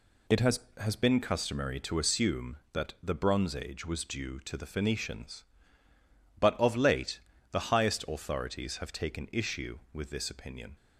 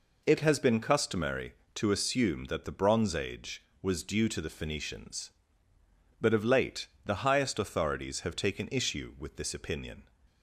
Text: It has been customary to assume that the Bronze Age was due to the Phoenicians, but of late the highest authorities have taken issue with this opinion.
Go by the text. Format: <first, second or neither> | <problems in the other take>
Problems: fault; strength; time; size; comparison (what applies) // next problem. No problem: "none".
second | says "has" twice; at 0.7 s // pauses between "late" and "the"; slight; at 7.2 s; 0.30 s long; slight in the second